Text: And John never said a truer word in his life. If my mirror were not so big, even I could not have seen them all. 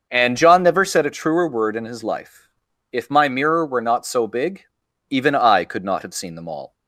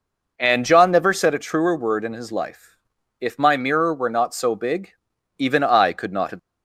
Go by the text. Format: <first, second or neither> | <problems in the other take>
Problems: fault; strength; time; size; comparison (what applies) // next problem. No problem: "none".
first | stops before "seen them all"; at 6.3 s